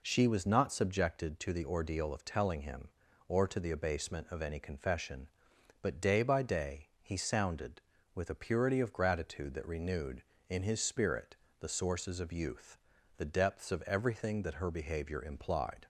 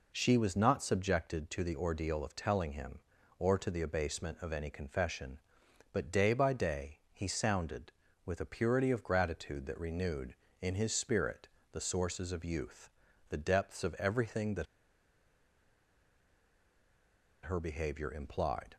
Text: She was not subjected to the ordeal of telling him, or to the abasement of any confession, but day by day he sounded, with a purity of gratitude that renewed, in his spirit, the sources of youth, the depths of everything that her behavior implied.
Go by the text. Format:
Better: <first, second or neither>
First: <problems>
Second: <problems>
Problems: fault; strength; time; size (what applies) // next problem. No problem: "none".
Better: first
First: pauses between "day" and "he"; slight; at 6.8 s; 0.16 s long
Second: pauses between "day" and "he"; slight; at 6.9 s; 0.16 s long // pauses between "that" and "her"; strong; at 14.6 s; 2.7 s long